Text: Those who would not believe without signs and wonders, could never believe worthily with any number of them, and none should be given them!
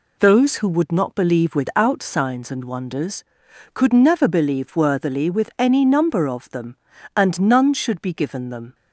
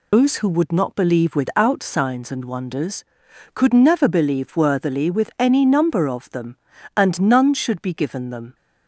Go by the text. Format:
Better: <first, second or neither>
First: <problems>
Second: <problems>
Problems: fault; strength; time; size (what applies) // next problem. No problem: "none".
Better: first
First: none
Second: loses the start of "Those"; at 0.1 s; 140 ms